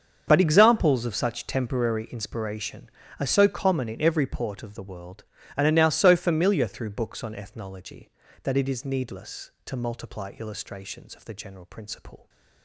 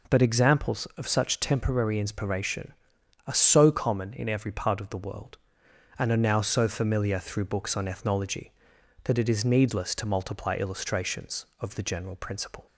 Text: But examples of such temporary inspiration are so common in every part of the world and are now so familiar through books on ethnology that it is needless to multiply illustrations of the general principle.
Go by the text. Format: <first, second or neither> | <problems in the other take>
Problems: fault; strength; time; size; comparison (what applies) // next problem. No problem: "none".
second | starts louder than the rest; until 1.2 s; 7 dB // says "port" for "part"; at 4.2 s